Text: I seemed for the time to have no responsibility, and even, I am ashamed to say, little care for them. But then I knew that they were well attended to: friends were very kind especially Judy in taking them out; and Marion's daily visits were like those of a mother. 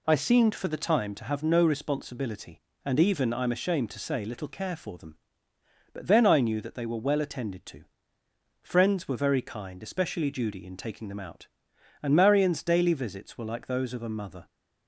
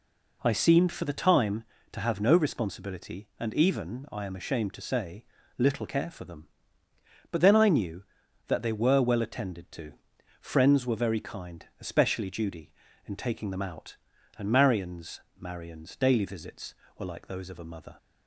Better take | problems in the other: first | pauses between "kind" and "especially"; slight; at 11.6 s; 0.16 s long // says "Marion's" twice; at 15.3 s

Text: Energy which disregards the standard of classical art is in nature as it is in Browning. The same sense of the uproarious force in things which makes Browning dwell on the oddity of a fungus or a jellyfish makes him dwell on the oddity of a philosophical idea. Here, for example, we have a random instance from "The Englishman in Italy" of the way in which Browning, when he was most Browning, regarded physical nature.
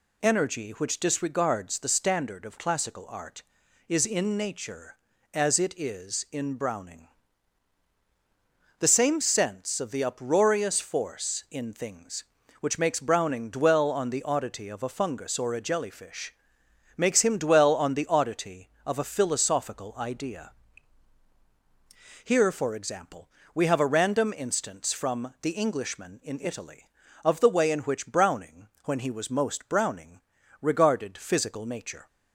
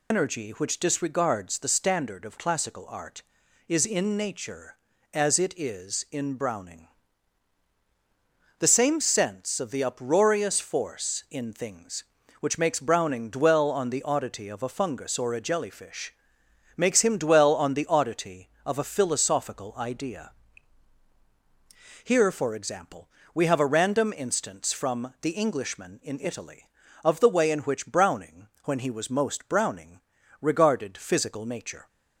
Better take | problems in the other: first | loses the start of "Energy"; at 0.1 s; 80 ms // pauses between "jellyfish" and "makes"; noticeable; at 16.1 s; 0.62 s long; noticeable in the first

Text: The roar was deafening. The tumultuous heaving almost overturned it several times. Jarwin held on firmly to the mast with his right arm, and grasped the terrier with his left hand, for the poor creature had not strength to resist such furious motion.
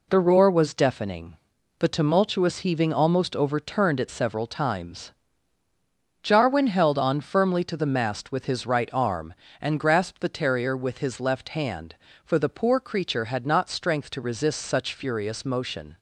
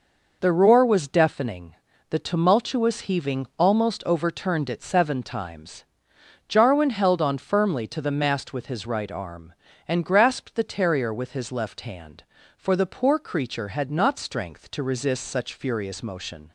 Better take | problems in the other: first | says "seven" for "several"; at 4.8 s

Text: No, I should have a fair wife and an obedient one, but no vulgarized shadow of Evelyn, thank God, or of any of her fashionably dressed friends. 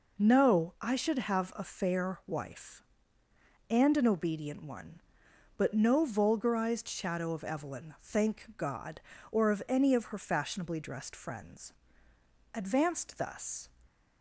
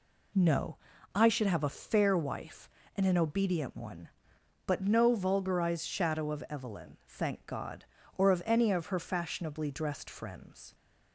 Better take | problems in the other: second | goes on to say "Advanced thus"; noticeable; from 12.5 s on; 1.1 s long

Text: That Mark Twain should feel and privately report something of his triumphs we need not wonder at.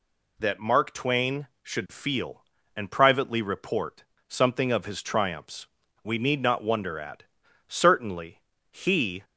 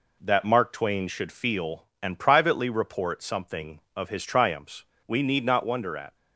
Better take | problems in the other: second | pauses between "report" and "something"; slight; at 4.0 s; 0.24 s long // pauses between "triumphs" and "we"; slight; at 5.6 s; 0.36 s long; slight in the second // goes on to say "Certainly he"; from 7.6 s on; 1.5 s long

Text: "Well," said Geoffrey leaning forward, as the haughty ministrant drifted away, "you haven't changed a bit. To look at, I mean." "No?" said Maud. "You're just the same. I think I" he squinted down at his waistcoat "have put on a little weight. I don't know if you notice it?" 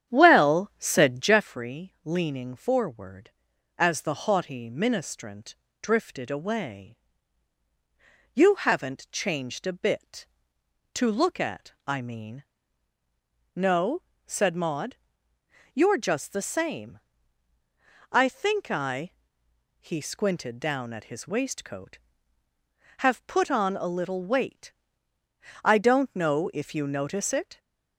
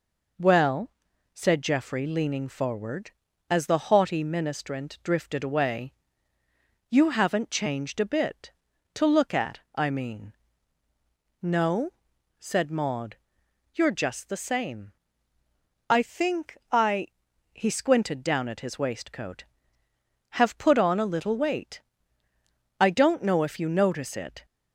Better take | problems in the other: second | starts louder than the rest; strong; until 1.5 s; 9.5 dB // pauses between "ministrant" and "drifted"; slight; at 5.5 s; 0.28 s long // pauses between "I" and "he"; noticeable; at 19.1 s; 0.70 s long; noticeable in the second

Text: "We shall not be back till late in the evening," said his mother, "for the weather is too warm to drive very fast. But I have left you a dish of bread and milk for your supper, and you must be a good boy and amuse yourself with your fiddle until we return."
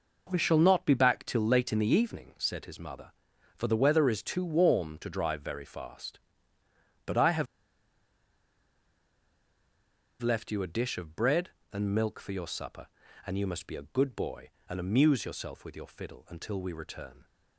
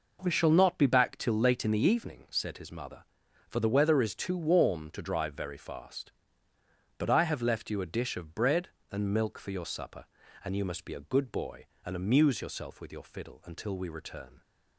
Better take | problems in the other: second | pauses between "have" and "left"; strong; at 7.4 s; 2.7 s long

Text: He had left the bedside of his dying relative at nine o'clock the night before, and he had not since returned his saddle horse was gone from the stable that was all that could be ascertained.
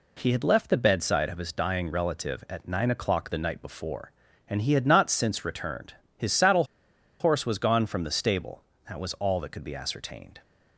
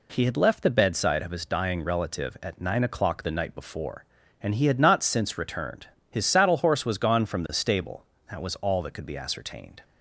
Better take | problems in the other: second | pauses between "returned" and "his"; slight; at 5.9 s; 0.22 s long; slight in the second // pauses between "saddle" and "horse"; noticeable; at 6.6 s; 0.56 s long

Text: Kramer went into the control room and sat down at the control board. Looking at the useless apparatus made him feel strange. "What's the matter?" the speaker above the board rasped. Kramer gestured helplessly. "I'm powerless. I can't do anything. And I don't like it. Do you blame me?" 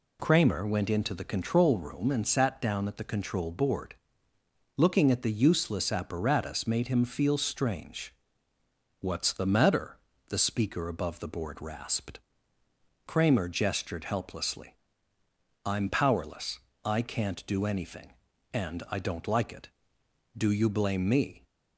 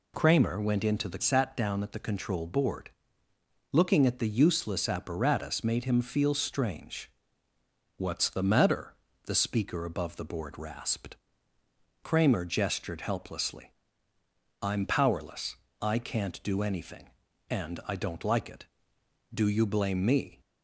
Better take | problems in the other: first | skips "control room and"; at 1.2 s

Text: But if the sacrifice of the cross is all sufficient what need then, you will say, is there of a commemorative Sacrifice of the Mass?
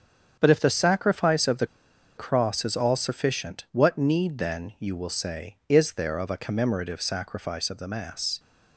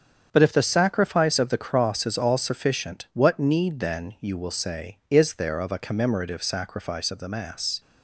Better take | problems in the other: second | starts louder than the rest; strong; until 1.4 s; 7 dB; strong in the second // pauses between "the" and "cross"; noticeable; at 1.6 s; 0.51 s long

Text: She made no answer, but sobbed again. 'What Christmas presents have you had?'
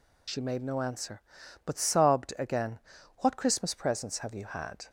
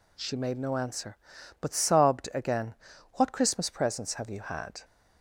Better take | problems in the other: second | loses the start of "She"; at 0.2 s; 45 ms

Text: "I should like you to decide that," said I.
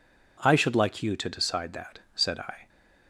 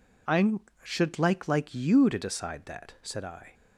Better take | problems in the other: first | says "like" twice; at 1.4 s

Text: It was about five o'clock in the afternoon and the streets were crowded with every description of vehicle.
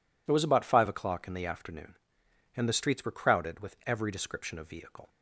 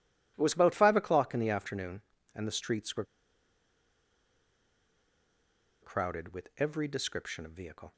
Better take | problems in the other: first | pauses between "were" and "crowded"; strong; at 3.0 s; 2.7 s long

